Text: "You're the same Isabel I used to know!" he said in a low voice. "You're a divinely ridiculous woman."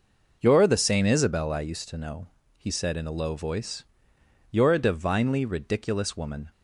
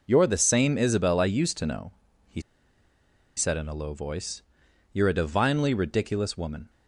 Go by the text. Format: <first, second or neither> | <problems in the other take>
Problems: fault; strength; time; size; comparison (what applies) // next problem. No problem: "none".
first | pauses between "he" and "said"; noticeable; at 2.4 s; 0.95 s long